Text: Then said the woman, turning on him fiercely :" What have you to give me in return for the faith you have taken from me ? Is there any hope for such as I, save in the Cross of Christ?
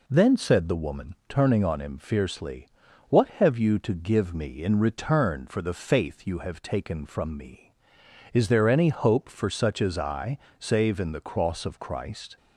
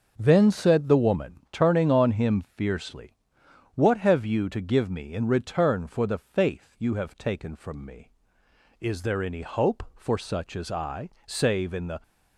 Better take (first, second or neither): first